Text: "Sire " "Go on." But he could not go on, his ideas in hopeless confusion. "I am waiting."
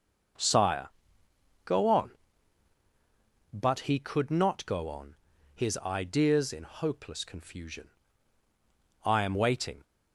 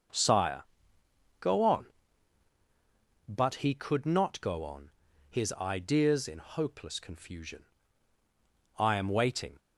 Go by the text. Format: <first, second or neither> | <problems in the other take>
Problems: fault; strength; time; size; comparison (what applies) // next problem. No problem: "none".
neither | none